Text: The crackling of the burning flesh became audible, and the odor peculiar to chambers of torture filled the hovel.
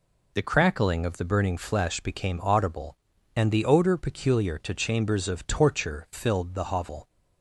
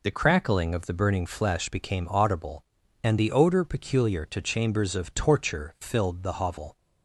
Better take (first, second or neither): neither